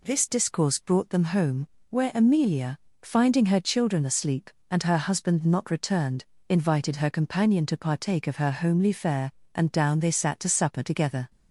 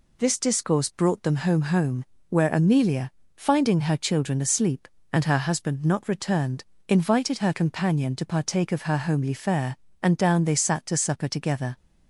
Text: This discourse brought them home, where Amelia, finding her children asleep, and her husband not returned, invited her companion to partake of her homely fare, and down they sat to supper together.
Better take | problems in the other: first | says "home" twice; at 1.6 s

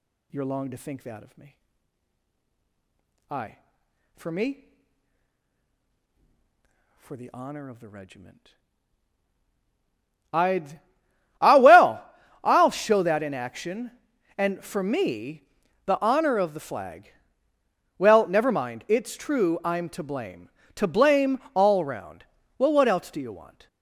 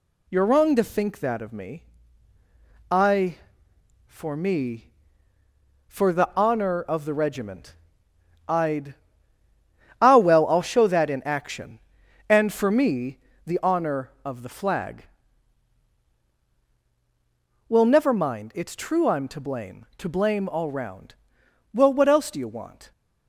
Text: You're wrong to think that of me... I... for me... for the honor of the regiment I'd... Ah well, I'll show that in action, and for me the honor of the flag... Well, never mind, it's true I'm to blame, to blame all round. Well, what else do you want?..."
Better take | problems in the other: second | says "long" for "wrong"; at 0.4 s // pauses between "regiment" and "I'd"; strong; at 8.5 s; 1.8 s long; noticeable in the second // pauses between "me" and "the"; at 15.4 s; 0.42 s long; slight in the second // pauses between "blame" and "all"; slight; at 21.3 s; 0.16 s long

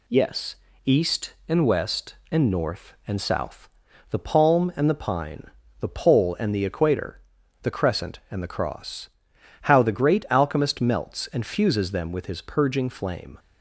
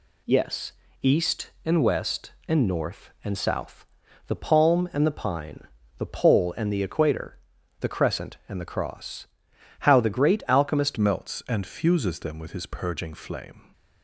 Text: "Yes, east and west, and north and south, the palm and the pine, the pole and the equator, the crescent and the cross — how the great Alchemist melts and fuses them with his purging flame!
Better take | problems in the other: first | changes voice at "melts"; from 10.9 s on; 2.7 s long

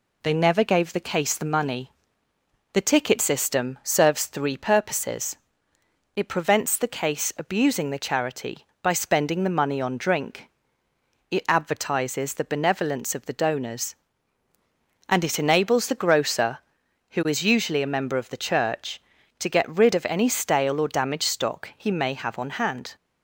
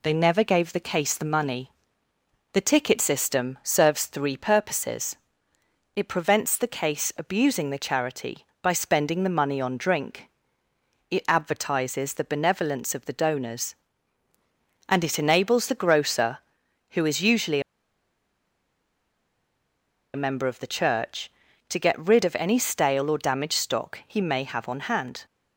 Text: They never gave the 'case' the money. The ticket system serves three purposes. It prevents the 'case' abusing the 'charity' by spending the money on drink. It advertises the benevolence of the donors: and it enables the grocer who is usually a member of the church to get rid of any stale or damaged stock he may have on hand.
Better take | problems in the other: first | pauses between "usually" and "a"; strong; at 17.5 s; 2.5 s long

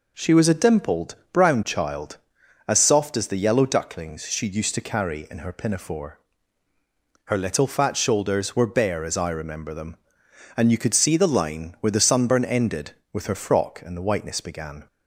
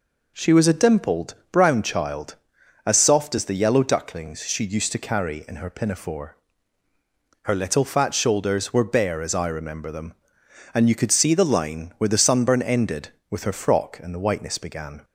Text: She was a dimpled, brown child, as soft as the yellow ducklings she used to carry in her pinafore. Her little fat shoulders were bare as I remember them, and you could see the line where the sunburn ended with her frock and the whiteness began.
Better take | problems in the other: neither | none

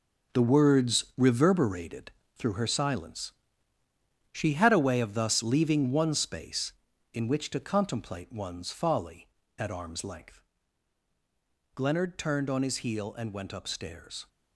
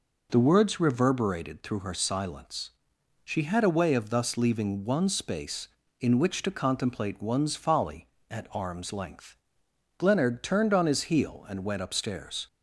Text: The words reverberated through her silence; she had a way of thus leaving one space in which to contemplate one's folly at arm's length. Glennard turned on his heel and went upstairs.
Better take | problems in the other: second | gets quieter; strong; throughout; 9.5 dB // pauses between "reverberated" and "through"; slight; at 2.1 s; 0.24 s long

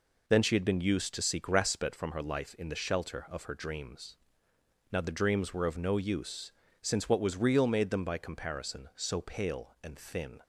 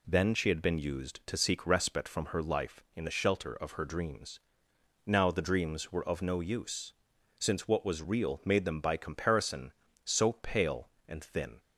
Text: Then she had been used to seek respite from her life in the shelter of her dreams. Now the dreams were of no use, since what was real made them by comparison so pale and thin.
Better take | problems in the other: neither | none

